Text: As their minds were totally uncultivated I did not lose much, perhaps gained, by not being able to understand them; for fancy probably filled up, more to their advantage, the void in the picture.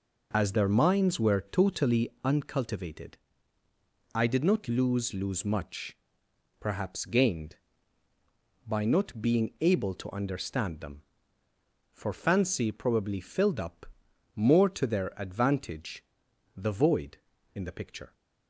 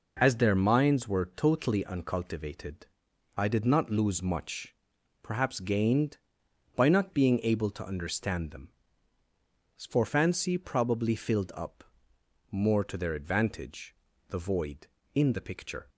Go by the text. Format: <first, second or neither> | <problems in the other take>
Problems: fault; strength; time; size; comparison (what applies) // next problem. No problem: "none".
second | pauses between "uncultivated" and "I"; noticeable; at 3.1 s; 0.96 s long; noticeable in the second // says "lose" twice; at 5.1 s